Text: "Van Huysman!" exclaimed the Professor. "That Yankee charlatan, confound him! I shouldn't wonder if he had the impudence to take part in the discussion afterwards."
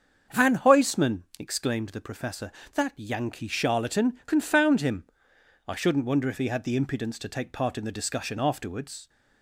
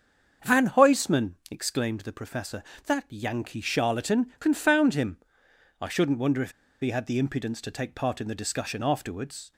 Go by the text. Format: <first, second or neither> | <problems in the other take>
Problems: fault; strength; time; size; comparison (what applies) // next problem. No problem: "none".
first | starts louder than the rest; until 1.5 s; 7 dB; also in the first // pauses between "if" and "he"; slight; at 6.5 s; 0.29 s long